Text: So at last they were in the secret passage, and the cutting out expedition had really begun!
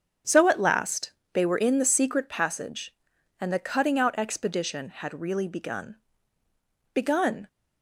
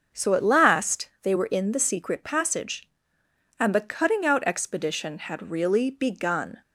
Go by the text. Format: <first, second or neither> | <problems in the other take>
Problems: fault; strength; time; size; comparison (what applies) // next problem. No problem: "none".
second | starts louder than the rest; until 1.4 s; 7 dB; also in the second // pauses between "last" and "they"; slight; at 1.1 s; 0.22 s long // says "begun" twice; at 6.9 s